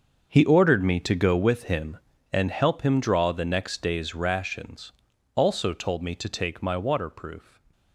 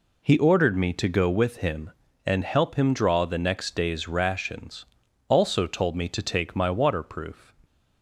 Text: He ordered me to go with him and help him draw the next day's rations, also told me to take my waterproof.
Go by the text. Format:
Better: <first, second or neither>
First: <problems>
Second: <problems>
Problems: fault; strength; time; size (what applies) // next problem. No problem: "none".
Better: second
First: gets quieter; strong; throughout; 14 dB // stays silent after the last word; slight; from 7.3 s on; 0.6 s long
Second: none